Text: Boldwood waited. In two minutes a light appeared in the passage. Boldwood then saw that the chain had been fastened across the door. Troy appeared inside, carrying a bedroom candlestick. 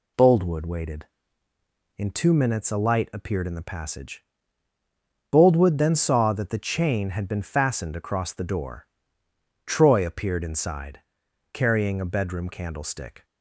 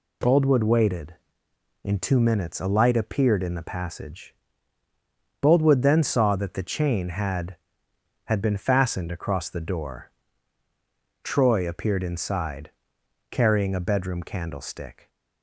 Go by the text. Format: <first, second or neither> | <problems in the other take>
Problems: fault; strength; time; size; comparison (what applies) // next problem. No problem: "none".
first | says "had" twice; at 8.2 s